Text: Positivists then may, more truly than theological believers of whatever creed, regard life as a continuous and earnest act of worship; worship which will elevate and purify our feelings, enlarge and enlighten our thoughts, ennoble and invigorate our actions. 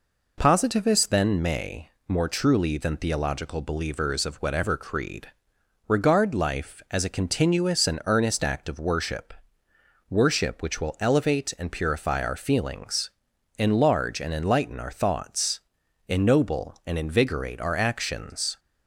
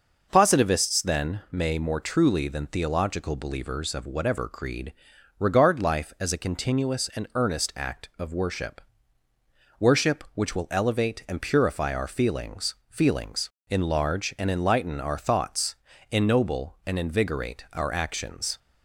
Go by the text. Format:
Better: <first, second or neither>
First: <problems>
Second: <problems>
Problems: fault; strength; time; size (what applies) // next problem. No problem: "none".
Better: first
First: none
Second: says "feelings" twice; at 12.9 s